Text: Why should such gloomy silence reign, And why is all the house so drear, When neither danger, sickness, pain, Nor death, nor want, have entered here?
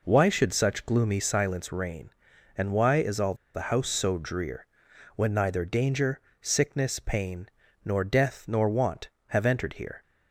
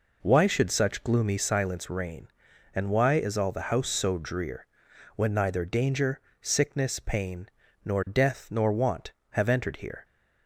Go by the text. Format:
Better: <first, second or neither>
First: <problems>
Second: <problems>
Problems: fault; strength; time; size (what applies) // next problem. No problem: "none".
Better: second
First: pauses between "all" and "the"; slight; at 3.3 s; 0.20 s long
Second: none